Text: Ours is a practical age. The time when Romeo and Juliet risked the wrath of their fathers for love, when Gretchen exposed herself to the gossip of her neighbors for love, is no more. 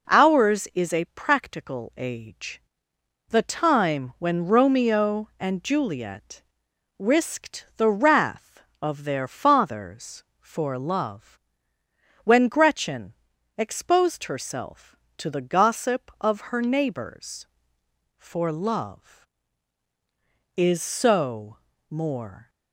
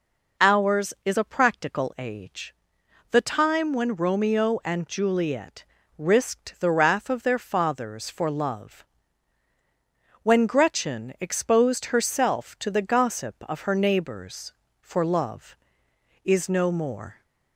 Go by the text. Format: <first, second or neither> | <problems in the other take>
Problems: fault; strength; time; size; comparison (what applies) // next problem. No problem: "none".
second | pauses between "Juliet" and "risked"; noticeable; at 6.4 s; 0.56 s long; slight in the second // pauses between "Gretchen" and "exposed"; at 13.1 s; 0.42 s long // says "so" for "no"; at 20.8 s